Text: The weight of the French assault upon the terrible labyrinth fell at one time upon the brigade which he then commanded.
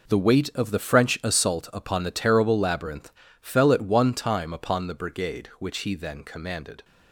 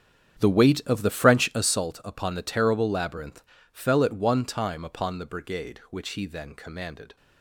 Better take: first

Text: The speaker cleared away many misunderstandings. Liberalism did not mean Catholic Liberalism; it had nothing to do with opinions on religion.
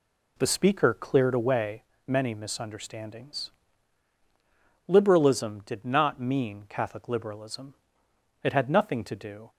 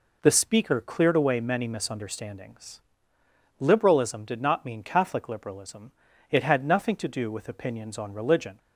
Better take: second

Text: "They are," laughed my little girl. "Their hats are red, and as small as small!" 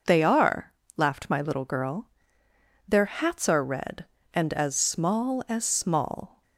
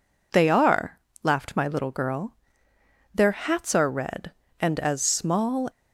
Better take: first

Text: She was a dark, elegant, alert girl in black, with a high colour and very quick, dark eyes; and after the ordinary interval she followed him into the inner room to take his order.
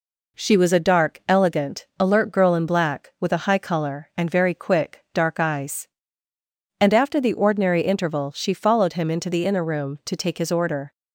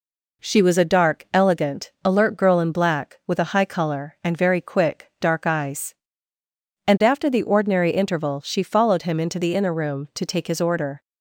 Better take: neither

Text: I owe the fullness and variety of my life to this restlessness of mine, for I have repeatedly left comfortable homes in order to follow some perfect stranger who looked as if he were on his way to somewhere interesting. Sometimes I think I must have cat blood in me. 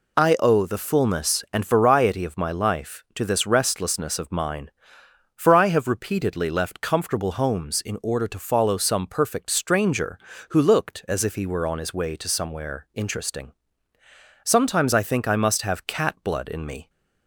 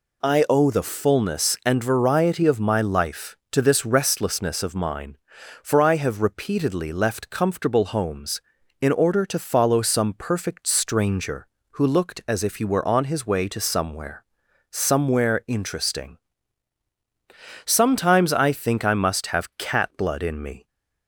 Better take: first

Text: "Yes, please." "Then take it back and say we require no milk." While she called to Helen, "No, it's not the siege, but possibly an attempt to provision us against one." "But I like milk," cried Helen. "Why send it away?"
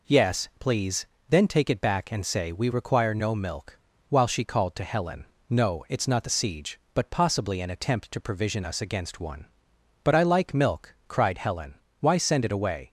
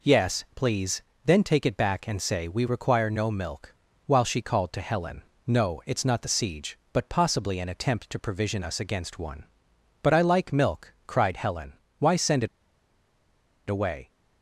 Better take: first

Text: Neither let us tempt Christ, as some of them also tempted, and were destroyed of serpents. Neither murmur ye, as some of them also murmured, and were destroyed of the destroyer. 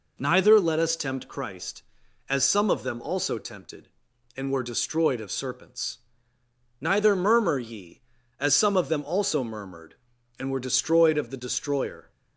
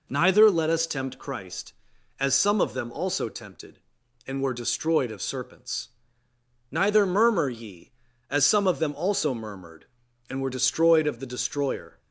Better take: neither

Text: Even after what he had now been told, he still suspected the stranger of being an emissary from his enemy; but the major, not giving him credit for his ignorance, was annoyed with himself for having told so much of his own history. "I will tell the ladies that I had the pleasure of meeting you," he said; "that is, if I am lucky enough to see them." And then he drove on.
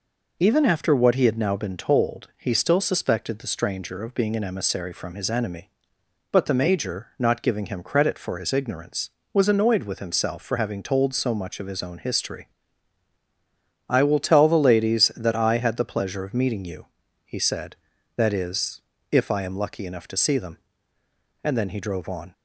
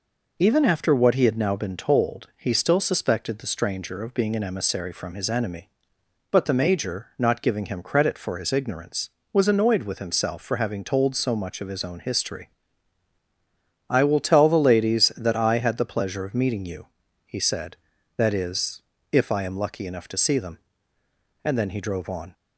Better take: neither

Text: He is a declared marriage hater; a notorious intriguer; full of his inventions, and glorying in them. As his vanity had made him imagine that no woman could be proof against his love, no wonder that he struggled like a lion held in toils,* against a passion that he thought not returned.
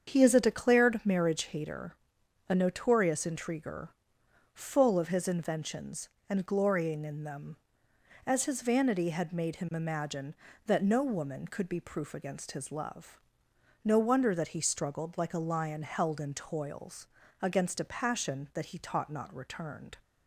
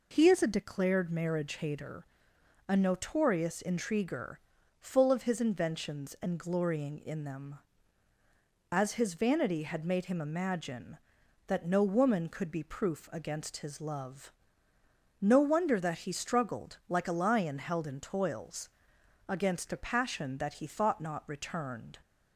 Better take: second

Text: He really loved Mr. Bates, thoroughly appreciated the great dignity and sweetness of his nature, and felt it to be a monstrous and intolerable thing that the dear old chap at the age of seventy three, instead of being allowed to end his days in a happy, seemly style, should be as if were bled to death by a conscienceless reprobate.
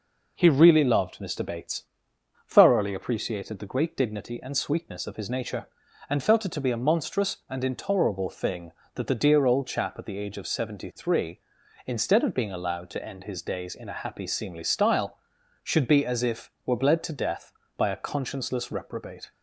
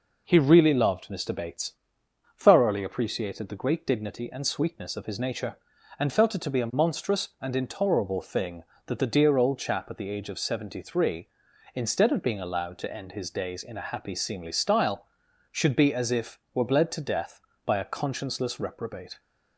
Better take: neither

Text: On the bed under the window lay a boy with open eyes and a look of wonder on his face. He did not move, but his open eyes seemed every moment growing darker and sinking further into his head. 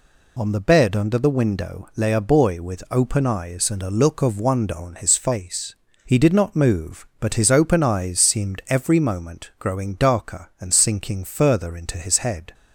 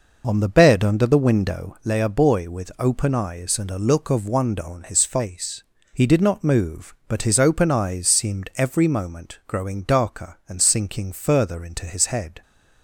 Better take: first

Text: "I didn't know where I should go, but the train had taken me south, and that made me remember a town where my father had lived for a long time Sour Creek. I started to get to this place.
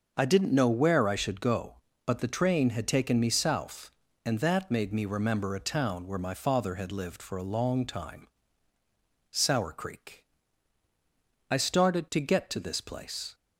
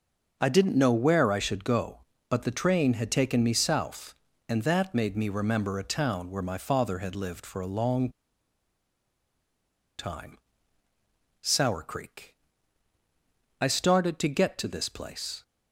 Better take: first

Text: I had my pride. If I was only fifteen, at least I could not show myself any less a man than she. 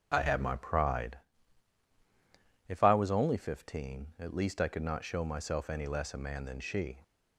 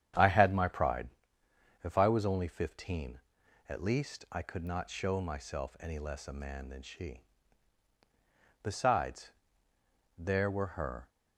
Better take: first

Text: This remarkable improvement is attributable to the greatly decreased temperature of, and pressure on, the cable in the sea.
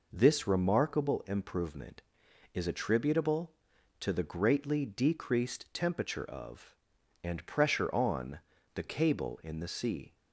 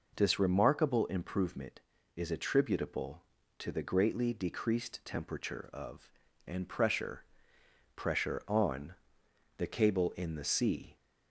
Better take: first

